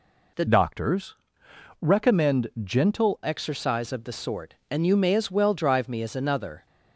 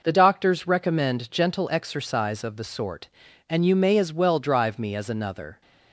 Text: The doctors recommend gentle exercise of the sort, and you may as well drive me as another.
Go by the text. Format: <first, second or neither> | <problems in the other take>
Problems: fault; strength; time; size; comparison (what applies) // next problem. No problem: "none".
second | changes voice from "doctors" to "gentle"; from 0.4 to 3.2 s; 2.8 s long // pauses between "doctors" and "recommend"; noticeable; at 1.1 s; 0.68 s long // pauses between "recommend" and "gentle"; slight; at 2.4 s; 0.16 s long